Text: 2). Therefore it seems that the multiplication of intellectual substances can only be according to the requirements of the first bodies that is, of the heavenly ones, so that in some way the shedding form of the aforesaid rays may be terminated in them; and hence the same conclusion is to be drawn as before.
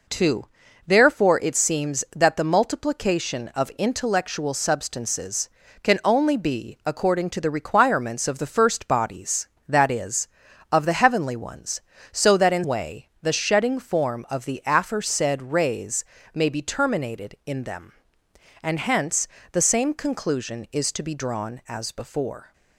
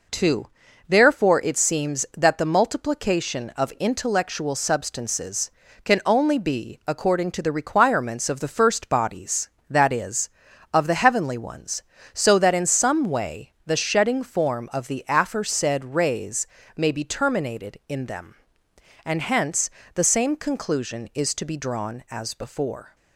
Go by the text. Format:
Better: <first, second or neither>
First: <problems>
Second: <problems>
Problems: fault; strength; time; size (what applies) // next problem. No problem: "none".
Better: second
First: skips "some"; at 12.6 s // pauses between "rays" and "may"; slight; at 16.0 s; 0.30 s long // pauses between "hence" and "the"; slight; at 19.2 s; 0.26 s long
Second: pauses between "rays" and "may"; slight; at 16.4 s; 0.30 s long // pauses between "hence" and "the"; slight; at 19.6 s; 0.26 s long